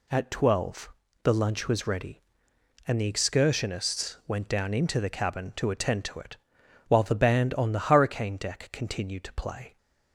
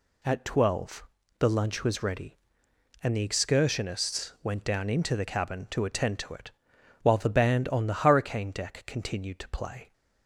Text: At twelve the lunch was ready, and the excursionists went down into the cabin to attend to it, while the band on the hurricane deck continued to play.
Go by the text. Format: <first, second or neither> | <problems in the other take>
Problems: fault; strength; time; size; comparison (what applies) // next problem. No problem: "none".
neither | pauses between "twelve" and "the"; slight; the same in both